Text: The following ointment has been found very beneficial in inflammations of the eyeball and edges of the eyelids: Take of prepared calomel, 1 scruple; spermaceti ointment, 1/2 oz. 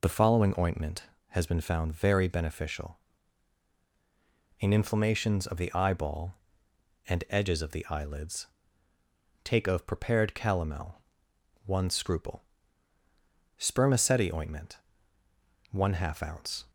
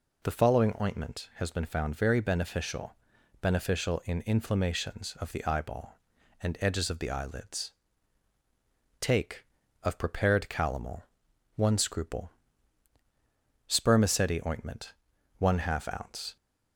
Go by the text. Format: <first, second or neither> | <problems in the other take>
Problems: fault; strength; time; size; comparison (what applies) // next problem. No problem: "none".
first | says "beneficial" twice; at 3.3 s